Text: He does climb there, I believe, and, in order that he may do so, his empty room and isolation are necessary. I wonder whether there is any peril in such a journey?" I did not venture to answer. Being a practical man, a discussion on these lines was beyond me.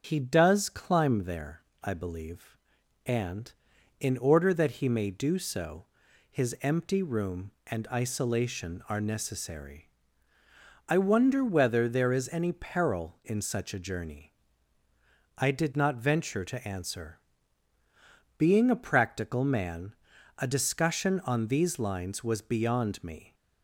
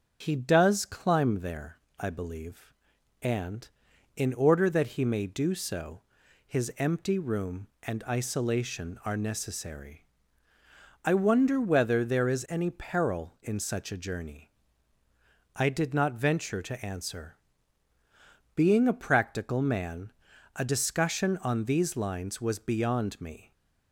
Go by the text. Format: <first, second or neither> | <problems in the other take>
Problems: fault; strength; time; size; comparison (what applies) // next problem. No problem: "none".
neither | starts louder than the rest; the same in both